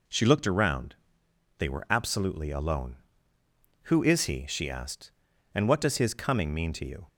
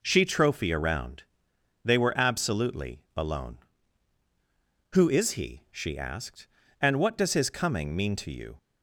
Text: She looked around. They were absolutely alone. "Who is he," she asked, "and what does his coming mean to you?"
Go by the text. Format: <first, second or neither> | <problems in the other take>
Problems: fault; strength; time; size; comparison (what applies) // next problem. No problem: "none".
first | says "trophy" for "looked"; at 0.2 s